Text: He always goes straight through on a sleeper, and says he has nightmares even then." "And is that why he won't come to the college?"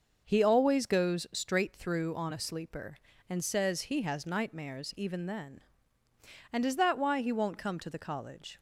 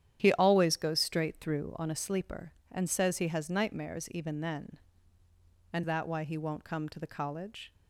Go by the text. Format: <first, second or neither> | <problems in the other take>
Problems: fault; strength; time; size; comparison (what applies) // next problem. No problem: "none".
first | starts louder than the rest; strong; until 1.2 s; 10 dB; also in the first // skips "is"; at 5.8 s